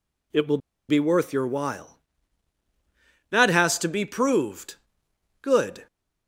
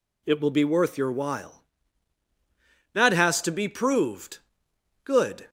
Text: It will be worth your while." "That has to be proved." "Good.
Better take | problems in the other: second | pauses between "will" and "be"; slight; at 0.5 s; 0.30 s long

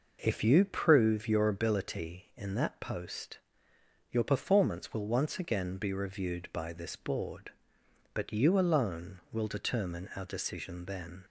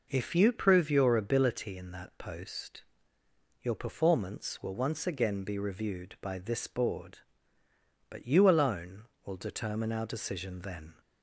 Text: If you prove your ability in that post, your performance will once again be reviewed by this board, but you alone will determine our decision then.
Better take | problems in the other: neither | none

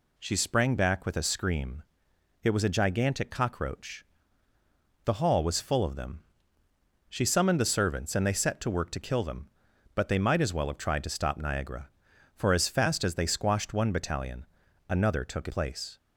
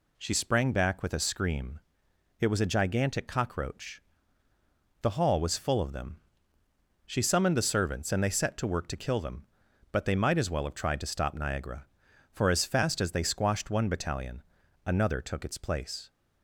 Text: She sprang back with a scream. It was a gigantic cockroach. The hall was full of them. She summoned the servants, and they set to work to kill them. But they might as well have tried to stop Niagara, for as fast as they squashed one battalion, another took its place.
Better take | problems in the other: second | skips "its"; at 15.4 s

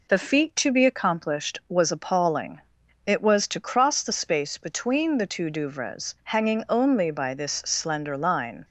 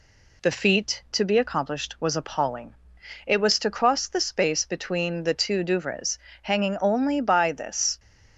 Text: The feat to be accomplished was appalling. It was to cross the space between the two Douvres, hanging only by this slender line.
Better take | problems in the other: first | stops before "slender line"; at 7.9 s

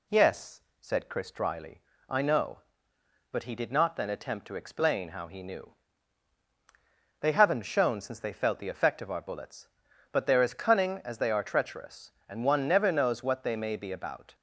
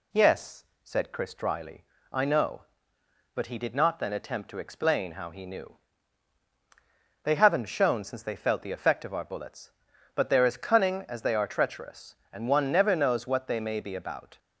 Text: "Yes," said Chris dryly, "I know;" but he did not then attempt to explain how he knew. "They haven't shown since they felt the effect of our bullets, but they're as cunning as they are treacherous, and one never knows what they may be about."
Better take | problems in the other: neither | none

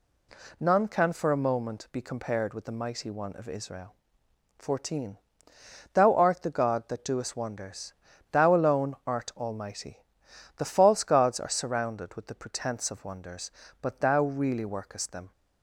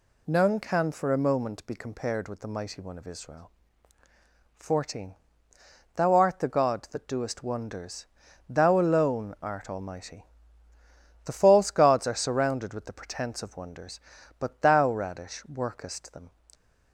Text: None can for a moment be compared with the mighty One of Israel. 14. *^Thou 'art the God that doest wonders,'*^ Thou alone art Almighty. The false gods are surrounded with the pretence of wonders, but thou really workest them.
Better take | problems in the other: first | says "radish" for "really"; at 14.9 s

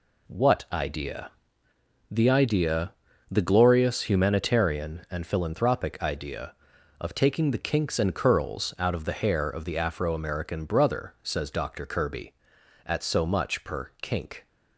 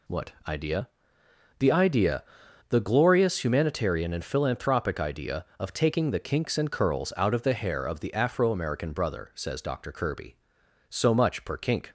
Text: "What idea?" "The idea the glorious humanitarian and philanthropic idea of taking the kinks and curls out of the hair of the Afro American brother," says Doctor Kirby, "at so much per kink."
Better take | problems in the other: first | pauses between "What" and "idea"; slight; at 0.3 s; 0.16 s long // pauses between "idea" and "the"; noticeable; at 2.2 s; 0.46 s long; slight in the first // skips "at"; at 10.6 s

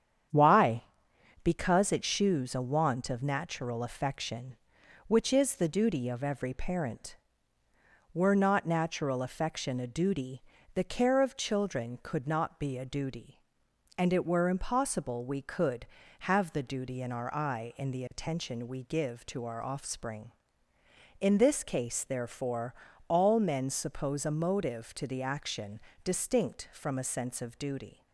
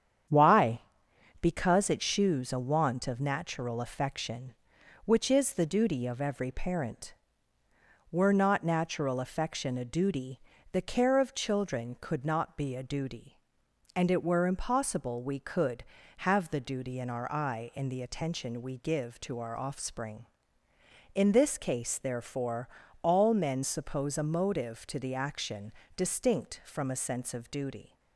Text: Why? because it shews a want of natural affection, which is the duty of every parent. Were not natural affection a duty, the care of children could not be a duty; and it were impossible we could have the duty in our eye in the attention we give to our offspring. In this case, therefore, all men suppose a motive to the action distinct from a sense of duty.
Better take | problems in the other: neither | starts louder than the rest; strong; the same in both // pauses between "action" and "distinct"; slight; the same in both

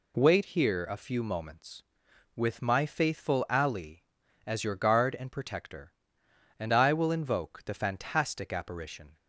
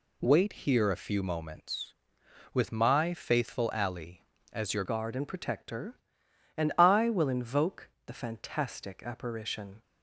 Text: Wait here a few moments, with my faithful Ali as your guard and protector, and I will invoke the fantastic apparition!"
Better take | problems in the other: first | changes voice at "guard"; from 4.8 s on; 5.0 s long // pauses between "invoke" and "the"; slight; at 7.8 s; 0.18 s long

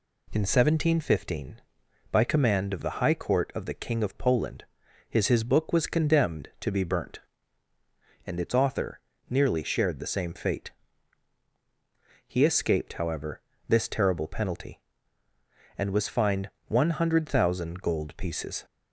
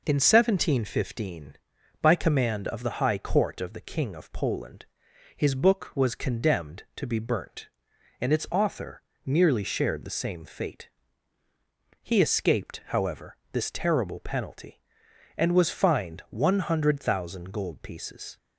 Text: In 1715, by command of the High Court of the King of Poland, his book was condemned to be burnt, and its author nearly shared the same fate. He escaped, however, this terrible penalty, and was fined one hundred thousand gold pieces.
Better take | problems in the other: second | says "his" twice; at 5.2 s // pauses between "author" and "nearly"; slight; at 8.9 s; 0.28 s long; slight in the second // pauses between "fined" and "one"; slight; at 16.5 s; 0.16 s long

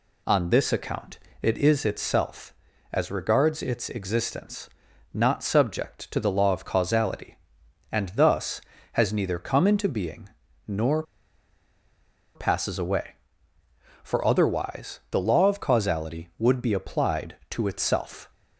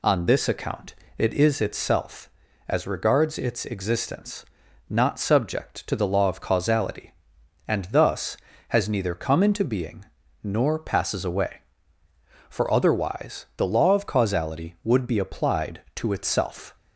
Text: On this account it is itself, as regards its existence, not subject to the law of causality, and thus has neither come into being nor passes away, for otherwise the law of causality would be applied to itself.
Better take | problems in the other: second | pauses between "account" and "it"; slight; at 1.1 s; 0.22 s long; slight in the second // pauses between "being" and "nor"; at 10.2 s; 0.38 s long; also in the second // pauses between "nor" and "passes"; strong; at 11.0 s; 1.3 s long

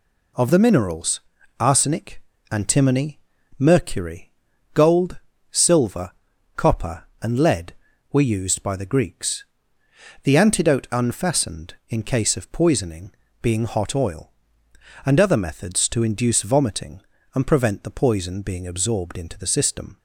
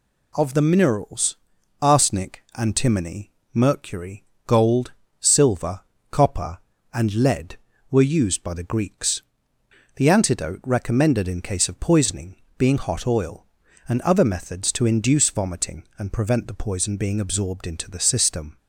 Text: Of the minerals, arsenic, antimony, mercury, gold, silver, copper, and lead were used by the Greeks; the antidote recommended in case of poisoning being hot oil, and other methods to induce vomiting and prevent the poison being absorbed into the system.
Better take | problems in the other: second | says "unfastened" for "recommended"; at 10.9 s // pauses between "poisoning" and "being"; slight; at 13.1 s; 0.30 s long; slight in the second

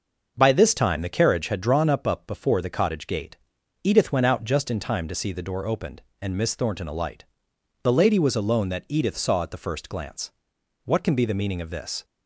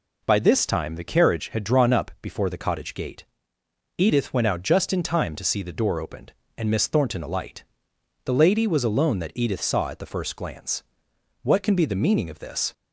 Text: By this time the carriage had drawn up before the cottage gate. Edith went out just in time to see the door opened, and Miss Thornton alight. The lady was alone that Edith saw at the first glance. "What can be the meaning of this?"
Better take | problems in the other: second | starts louder than the rest; noticeable; until 1.3 s; 6 dB // says "up" twice; at 2.0 s

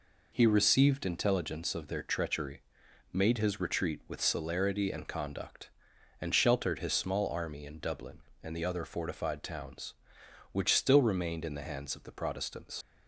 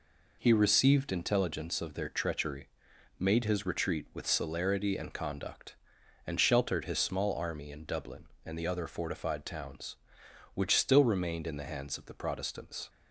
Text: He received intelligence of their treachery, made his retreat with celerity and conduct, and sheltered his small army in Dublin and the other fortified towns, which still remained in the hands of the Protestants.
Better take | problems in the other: second | leaves "Protestants" unfinished; at 12.8 s; 60 ms

